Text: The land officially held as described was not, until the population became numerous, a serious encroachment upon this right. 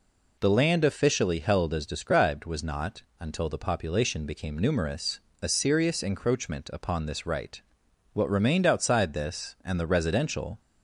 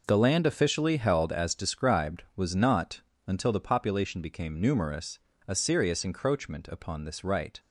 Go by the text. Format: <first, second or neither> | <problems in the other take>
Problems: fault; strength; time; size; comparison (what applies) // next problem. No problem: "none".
second | goes on to say "What remained outside this and the residential"; strong; from 8.1 s on; 2.4 s long